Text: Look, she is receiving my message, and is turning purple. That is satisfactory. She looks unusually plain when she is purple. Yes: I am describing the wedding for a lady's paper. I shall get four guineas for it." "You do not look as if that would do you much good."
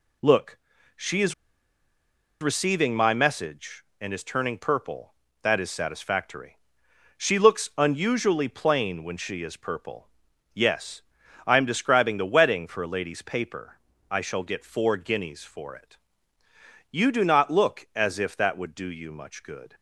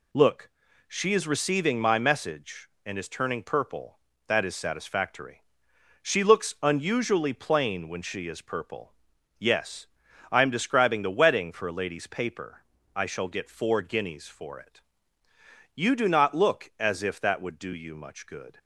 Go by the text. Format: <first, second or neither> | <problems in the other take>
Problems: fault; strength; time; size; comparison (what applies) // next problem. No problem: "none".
second | pauses between "is" and "receiving"; at 1.3 s; 1.0 s long